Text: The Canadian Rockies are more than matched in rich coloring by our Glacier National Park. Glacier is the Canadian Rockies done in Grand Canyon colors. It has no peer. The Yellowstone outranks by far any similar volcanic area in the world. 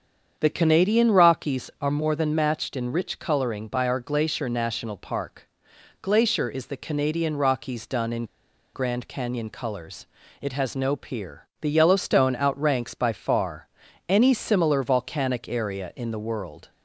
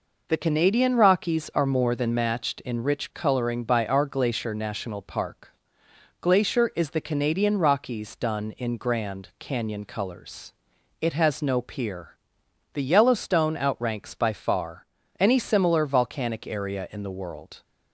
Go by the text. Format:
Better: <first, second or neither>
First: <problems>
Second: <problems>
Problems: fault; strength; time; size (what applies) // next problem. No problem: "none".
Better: second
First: starts louder than the rest; strong; until 1.4 s; 7.5 dB // pauses between "in" and "Grand"; noticeable; at 8.2 s; 0.48 s long // pauses between "far" and "any"; at 13.6 s; 0.40 s long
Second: pauses between "far" and "any"; slight; at 14.8 s; 0.34 s long